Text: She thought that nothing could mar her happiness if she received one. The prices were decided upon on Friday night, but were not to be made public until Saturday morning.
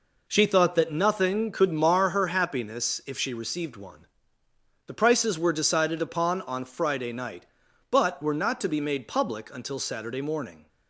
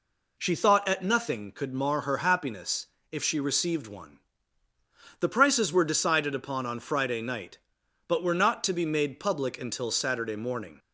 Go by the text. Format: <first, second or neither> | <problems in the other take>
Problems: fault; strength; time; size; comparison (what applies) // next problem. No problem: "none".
first | says "at" for "that"; at 0.8 s // pauses between "happiness" and "if"; slight; at 2.8 s; 0.24 s long